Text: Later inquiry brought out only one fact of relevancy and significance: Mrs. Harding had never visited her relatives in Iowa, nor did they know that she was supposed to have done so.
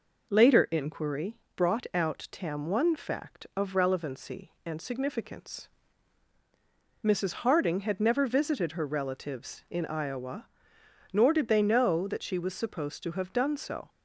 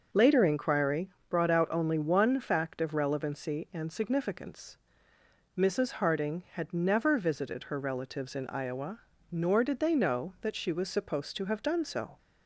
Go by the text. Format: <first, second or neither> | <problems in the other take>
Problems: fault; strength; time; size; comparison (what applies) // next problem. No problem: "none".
second | pauses between "inquiry" and "brought"; slight; at 1.3 s; 0.18 s long; slight in the second // says "tam" for "only"; at 2.3 s